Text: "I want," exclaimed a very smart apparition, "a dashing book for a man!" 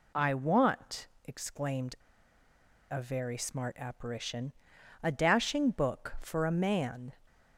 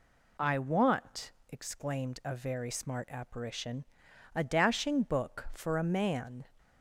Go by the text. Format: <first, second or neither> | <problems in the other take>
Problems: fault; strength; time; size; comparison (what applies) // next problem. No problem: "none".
second | pauses between "exclaimed" and "a"; noticeable; at 1.9 s; 0.95 s long